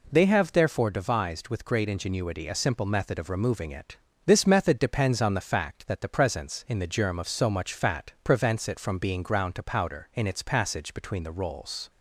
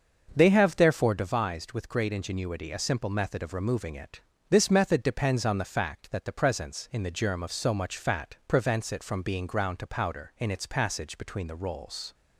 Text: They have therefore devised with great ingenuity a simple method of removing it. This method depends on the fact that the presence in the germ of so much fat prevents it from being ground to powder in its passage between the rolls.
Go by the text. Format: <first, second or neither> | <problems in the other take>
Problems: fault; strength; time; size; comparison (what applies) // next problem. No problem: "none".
first | starts louder than the rest; until 1.4 s; 6.5 dB